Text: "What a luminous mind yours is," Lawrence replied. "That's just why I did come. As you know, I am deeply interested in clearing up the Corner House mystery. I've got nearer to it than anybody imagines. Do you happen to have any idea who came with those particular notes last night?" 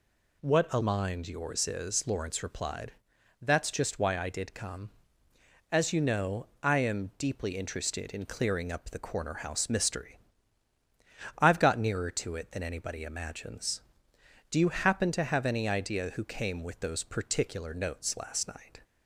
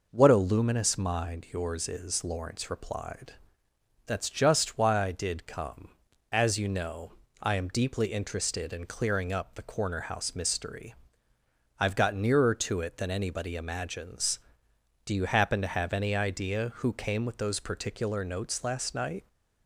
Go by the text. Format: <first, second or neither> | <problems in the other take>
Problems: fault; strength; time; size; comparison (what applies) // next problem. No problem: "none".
second | skips "luminous"; at 0.7 s